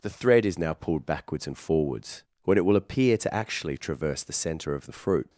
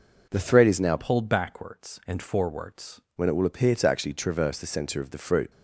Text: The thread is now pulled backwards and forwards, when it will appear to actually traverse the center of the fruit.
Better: first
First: none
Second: changes voice from "pulled" to "forwards"; from 0.9 to 3.0 s; 2.1 s long

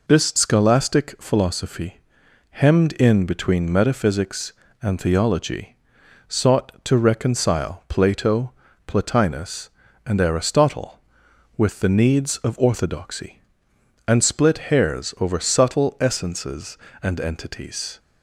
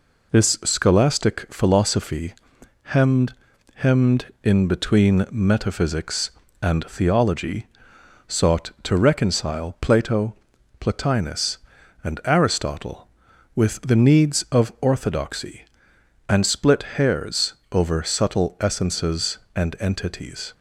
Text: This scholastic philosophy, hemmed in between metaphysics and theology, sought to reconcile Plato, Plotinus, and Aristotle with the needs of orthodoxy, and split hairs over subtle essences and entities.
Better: first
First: none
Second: says "hemmed" twice; at 3.7 s // pauses between "hairs" and "over"; slight; at 17.5 s; 0.18 s long

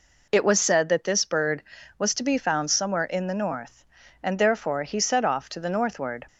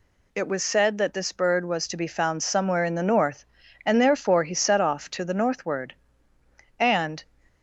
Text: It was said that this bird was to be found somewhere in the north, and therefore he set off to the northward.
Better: first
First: none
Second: goes on to say "And"; slight; from 6.7 s on; 0.46 s long

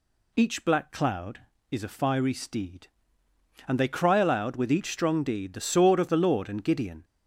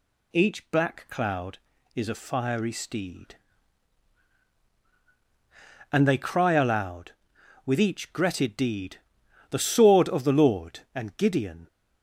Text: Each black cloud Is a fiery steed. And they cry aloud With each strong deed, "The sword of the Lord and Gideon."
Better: first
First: none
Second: says "gretted" for "strong"; at 8.1 s

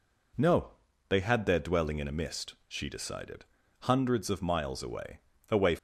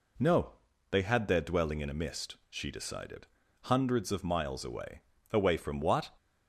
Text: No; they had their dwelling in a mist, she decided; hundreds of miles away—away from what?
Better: second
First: stops before "from what"; at 5.7 s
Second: none

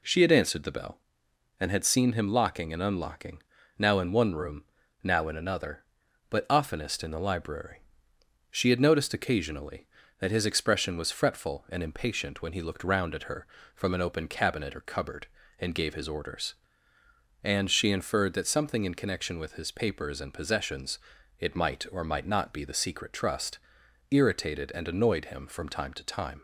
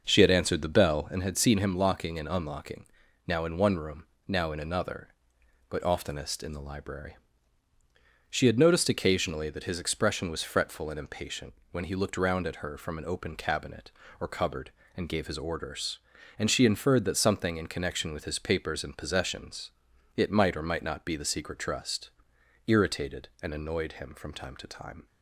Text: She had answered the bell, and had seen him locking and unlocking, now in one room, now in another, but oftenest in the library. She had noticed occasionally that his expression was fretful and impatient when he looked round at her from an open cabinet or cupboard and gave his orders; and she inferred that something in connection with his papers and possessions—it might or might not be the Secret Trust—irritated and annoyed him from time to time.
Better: first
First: none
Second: starts louder than the rest; noticeable; until 1.3 s; 6 dB // pauses between "impatient" and "when"; slight; at 11.5 s; 0.18 s long

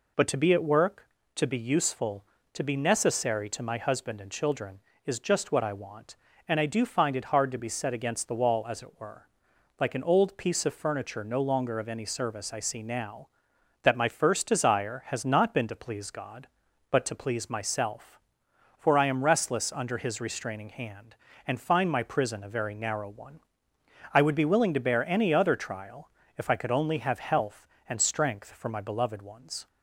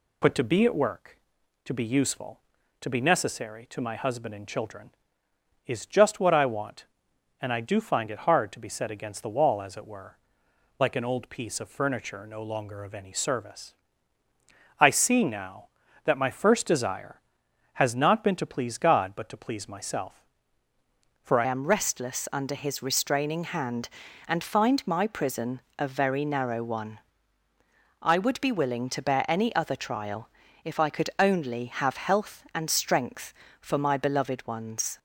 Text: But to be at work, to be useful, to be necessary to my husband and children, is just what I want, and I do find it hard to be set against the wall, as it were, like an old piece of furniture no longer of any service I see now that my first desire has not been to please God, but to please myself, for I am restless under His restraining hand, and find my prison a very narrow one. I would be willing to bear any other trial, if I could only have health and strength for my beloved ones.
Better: first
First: none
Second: pauses between "service" and "I"; at 13.7 s; 1.0 s long // changes voice at "am"; from 21.4 s on; 13.5 s long // pauses between "prison" and "a"; slight; at 25.5 s; 0.18 s long

